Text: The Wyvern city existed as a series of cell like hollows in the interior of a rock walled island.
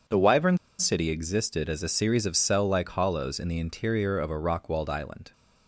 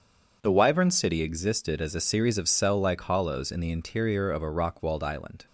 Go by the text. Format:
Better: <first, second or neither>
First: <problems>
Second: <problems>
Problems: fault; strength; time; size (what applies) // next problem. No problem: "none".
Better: second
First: starts louder than the rest; until 1.3 s; 7 dB // pauses between "Wyvern" and "city"; slight; at 0.5 s; 0.22 s long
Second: starts louder than the rest; until 1.4 s; 7 dB